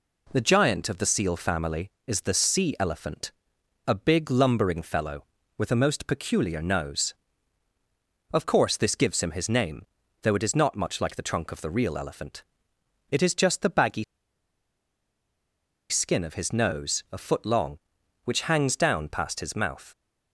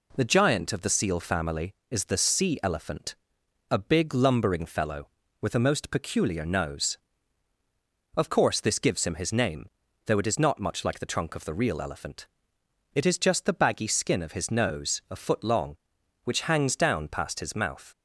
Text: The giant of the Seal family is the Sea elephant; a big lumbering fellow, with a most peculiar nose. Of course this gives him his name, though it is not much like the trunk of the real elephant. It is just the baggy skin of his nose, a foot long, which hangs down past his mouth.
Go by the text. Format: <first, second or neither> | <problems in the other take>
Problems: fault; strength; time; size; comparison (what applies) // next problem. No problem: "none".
second | pauses between "baggy" and "skin"; strong; at 14.0 s; 1.8 s long